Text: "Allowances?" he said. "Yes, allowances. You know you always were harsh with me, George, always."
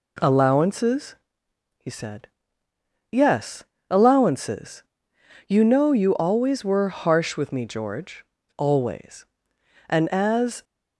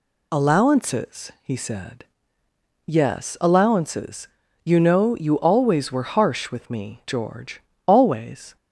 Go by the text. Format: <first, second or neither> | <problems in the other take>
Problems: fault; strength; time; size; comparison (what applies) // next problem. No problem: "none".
second | goes on to say "And as"; noticeable; from 9.8 s on; 0.76 s long